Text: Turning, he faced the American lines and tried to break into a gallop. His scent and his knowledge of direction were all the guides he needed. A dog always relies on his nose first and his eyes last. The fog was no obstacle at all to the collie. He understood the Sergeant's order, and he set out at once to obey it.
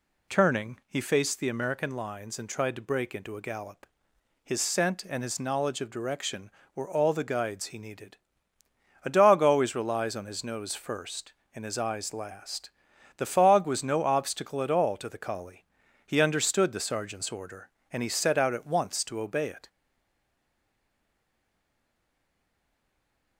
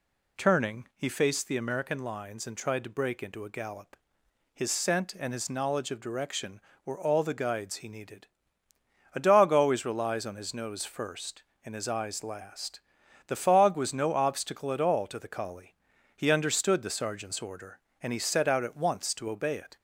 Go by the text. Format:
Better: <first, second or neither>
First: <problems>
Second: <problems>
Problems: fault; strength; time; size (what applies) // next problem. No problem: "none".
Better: second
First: stays silent after the last word; strong; from 19.6 s on; 3.7 s long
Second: none